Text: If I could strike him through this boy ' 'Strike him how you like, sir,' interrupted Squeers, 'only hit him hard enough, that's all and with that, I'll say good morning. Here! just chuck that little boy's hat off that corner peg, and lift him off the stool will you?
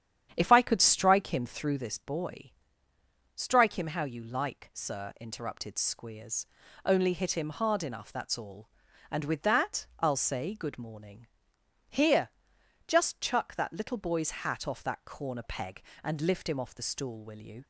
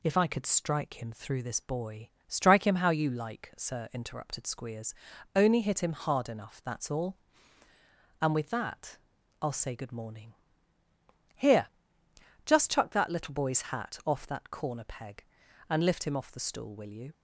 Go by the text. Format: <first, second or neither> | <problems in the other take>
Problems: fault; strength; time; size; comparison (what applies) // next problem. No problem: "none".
second | starts louder than the rest; strong; until 2.1 s; 9.5 dB